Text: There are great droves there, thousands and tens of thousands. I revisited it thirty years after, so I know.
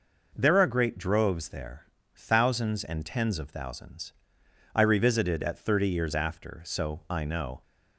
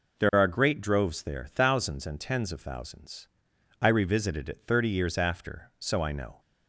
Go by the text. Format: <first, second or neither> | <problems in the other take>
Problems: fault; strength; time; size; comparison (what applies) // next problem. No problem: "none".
second | says "at" for "it"; at 5.4 s